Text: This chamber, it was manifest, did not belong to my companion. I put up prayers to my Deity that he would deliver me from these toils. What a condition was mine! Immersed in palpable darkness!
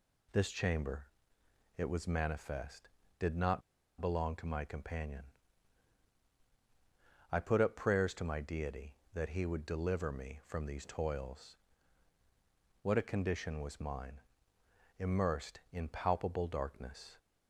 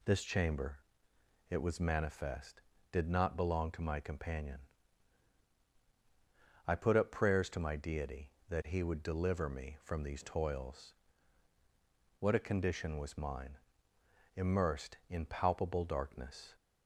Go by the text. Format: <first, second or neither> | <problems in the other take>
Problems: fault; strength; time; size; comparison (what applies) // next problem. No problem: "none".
second | pauses between "not" and "belong"; at 3.6 s; 0.39 s long